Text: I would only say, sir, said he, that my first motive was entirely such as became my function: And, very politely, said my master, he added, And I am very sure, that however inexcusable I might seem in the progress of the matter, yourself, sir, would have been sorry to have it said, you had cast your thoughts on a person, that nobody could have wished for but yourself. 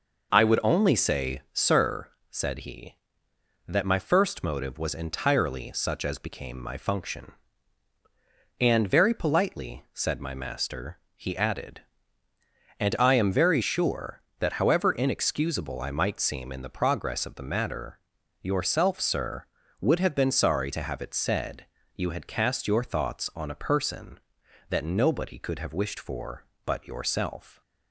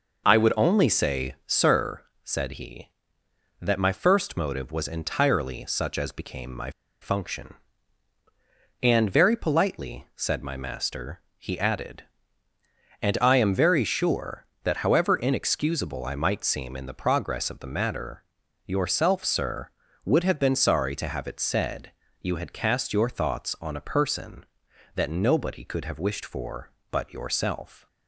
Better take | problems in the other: first | pauses between "my" and "function"; slight; at 6.6 s; 0.31 s long

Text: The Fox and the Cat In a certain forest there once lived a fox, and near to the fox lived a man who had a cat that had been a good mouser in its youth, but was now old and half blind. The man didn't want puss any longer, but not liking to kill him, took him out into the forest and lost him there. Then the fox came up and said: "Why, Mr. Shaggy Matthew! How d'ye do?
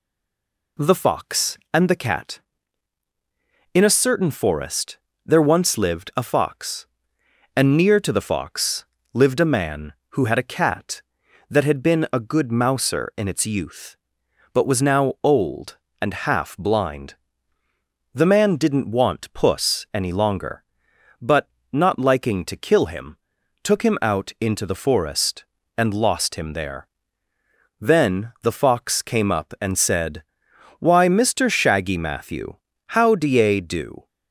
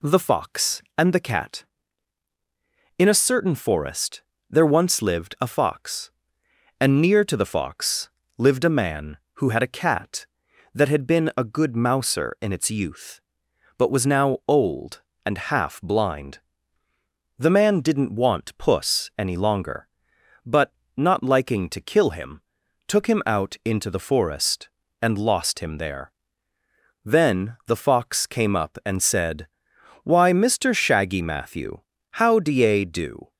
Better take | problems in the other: second | stays silent before the first word; slight; until 0.7 s; 0.7 s long // pauses between "forest" and "there"; slight; at 4.9 s; 0.26 s long; slight in the second // pauses between "fox" and "lived"; slight; at 8.8 s; 0.30 s long; slight in the second // pauses between "but" and "not"; slight; at 21.4 s; 0.24 s long; slight in the second

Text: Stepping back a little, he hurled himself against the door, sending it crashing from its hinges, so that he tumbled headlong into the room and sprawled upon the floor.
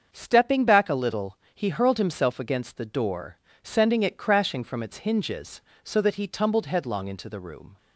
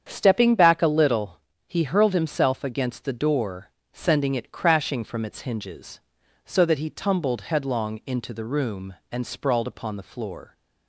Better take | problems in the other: second | starts louder than the rest; until 1.1 s; 7 dB; strong in the second // stops before "and sprawled upon the floor"; at 7.7 s

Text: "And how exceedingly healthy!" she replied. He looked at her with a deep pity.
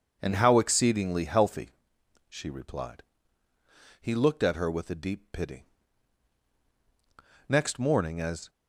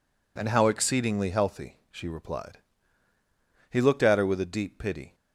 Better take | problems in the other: second | goes on to say "Next morning as"; noticeable; from 7.4 s on; 1.0 s long

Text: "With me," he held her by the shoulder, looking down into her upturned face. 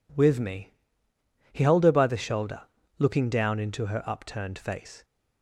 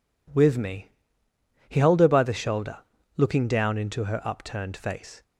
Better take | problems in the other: neither | none

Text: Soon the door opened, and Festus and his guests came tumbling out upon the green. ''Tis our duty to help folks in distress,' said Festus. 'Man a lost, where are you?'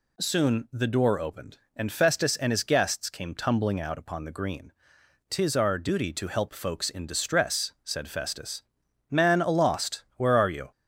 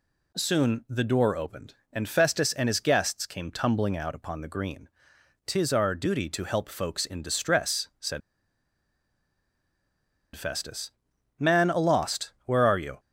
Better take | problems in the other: first | pauses between "said" and "Festus"; strong; at 8.2 s; 2.1 s long

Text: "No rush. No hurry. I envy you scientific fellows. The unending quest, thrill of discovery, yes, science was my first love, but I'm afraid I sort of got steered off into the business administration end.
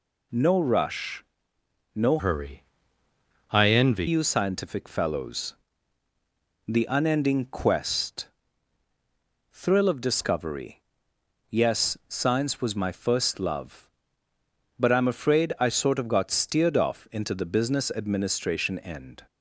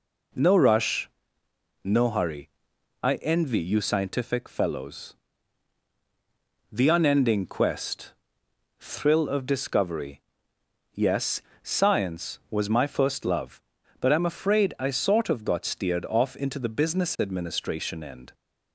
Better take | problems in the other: second | changes voice from "hurry" to "envy"; from 2.1 to 4.0 s; 1.9 s long

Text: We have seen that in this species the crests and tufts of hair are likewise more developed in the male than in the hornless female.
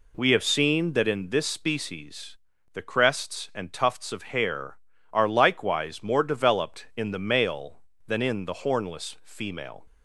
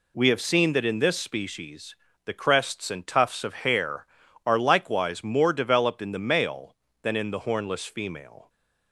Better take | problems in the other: neither | pauses between "species" and "the"; slight; the same in both

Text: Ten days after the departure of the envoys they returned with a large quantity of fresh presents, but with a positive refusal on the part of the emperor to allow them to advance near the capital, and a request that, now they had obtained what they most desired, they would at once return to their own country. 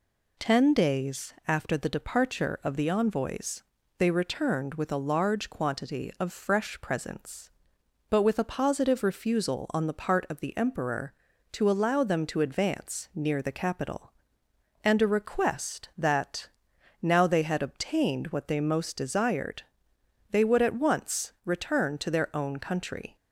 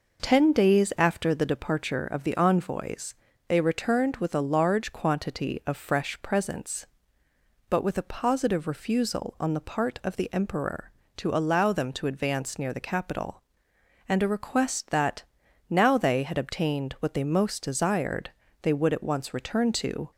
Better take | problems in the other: first | pauses between "envoys" and "they"; slight; at 3.1 s; 0.32 s long; slight in the first // stops before "their own country"; at 20.1 s

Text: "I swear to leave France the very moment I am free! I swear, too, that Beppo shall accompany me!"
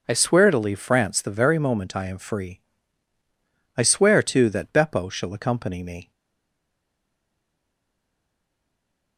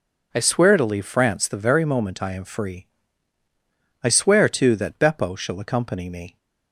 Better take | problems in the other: second | stays silent after the last word; strong; from 6.1 s on; 3.0 s long

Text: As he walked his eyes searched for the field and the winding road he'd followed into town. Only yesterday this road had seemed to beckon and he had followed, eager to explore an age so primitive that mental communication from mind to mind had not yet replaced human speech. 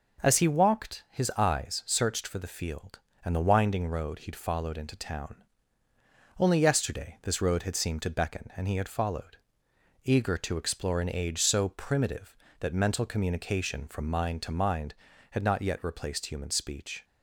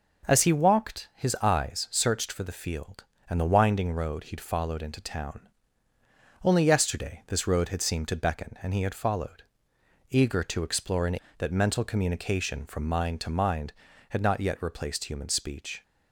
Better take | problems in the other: first | skips "age so primitive"; at 11.2 s

